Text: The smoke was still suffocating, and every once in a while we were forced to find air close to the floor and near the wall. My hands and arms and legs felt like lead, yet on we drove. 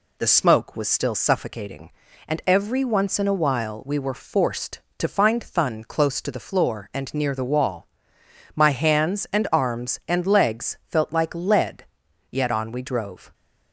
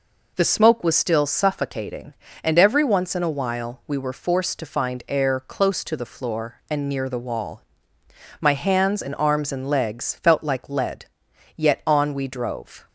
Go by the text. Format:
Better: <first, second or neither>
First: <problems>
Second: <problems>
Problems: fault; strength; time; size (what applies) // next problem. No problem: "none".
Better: second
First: says "thun" for "air"; at 5.4 s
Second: none